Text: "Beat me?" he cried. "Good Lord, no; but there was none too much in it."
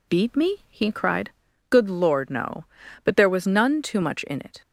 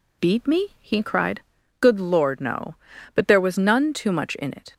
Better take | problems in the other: neither | none

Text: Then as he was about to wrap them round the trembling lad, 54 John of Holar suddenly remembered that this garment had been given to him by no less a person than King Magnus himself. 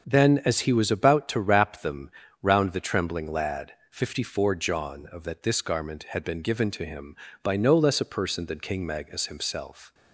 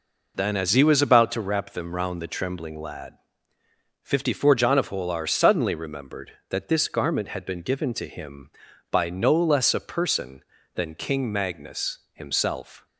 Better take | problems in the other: second | pauses between "them" and "round"; slight; at 2.1 s; 0.32 s long // skips "Holar suddenly remembered"; at 5.2 s

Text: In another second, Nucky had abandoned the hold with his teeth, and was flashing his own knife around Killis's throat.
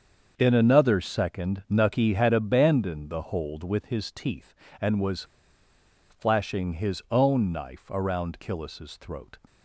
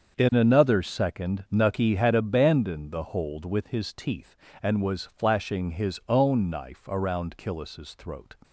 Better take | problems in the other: second | starts louder than the rest; until 1.3 s; 7 dB; also in the second // pauses between "was" and "flashing"; noticeable; at 5.2 s; 0.87 s long

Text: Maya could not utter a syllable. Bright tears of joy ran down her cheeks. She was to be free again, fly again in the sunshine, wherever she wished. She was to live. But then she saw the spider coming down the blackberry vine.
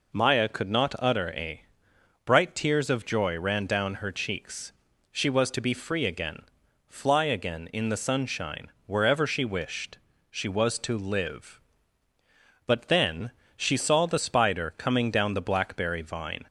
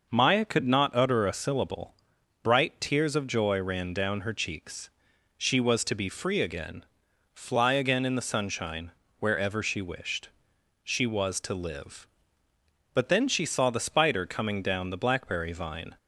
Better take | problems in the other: second | skips "syllable"; at 1.9 s // pauses between "then" and "she"; slight; at 13.3 s; 0.26 s long

